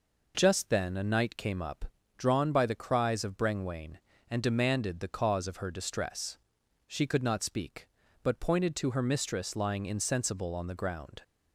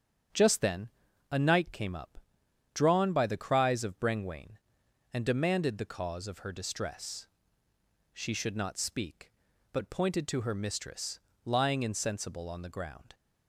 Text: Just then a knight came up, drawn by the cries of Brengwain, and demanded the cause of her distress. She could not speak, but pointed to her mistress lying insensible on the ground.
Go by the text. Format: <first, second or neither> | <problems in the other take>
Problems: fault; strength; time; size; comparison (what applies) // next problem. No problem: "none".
first | starts louder than the rest; strong; until 1.7 s; 8 dB // pauses between "then" and "a"; at 0.8 s; 0.42 s long // says "should" for "could"; at 8.3 s // pauses between "mistress" and "lying"; slight; at 11.1 s; 0.26 s long